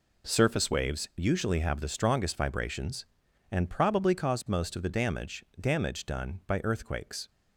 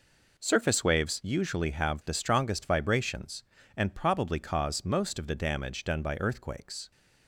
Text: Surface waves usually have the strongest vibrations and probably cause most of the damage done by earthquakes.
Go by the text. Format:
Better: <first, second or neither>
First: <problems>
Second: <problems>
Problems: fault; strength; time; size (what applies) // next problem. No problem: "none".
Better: second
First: says "damage" twice; at 5.5 s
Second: none